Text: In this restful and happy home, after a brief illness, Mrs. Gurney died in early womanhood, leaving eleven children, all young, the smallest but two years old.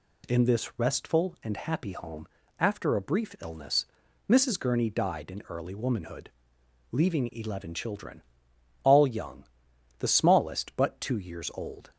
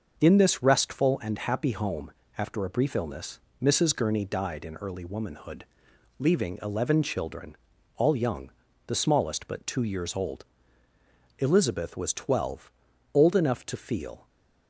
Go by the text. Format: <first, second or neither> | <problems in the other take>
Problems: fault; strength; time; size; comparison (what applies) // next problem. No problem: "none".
first | starts louder than the rest; noticeable; until 1.1 s; 6 dB // goes on to say "Elizabeth was twelve old enough to feel"; strong; from 11.4 s on; 2.8 s long